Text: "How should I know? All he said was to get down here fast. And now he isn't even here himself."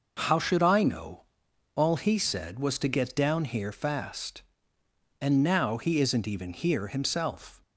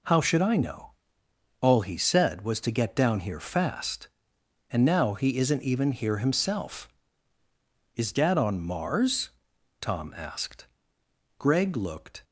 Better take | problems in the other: first | goes on to say "Is Dad on Mars Tom asked Greg looked"; strong; from 7.9 s on; 4.2 s long

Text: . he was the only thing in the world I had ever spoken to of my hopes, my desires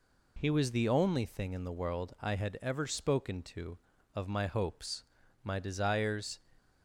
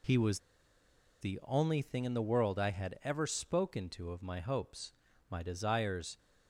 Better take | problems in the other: first | pauses between "was" and "the"; noticeable; at 0.4 s; 0.81 s long

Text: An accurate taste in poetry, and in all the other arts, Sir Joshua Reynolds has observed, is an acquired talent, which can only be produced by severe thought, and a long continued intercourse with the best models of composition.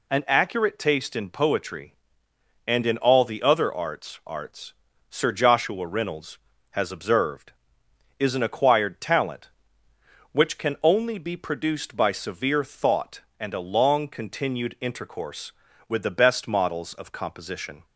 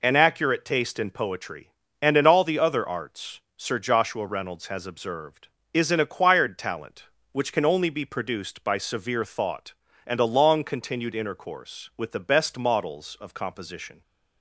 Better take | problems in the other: second | says "arts" twice; at 4.2 s

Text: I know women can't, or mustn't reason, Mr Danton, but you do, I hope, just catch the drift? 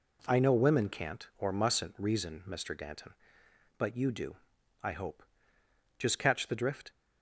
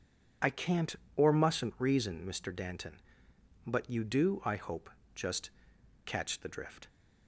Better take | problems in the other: first | skips "know women"; at 0.4 s // pauses between "just" and "catch"; noticeable; at 5.4 s; 0.54 s long

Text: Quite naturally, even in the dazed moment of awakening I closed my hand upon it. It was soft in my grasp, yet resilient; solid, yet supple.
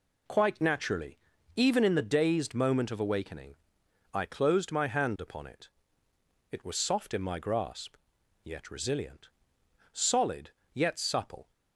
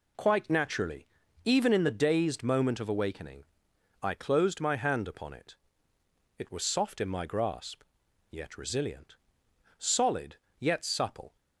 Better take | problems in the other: neither | pauses between "awakening" and "I"; noticeable; the same in both

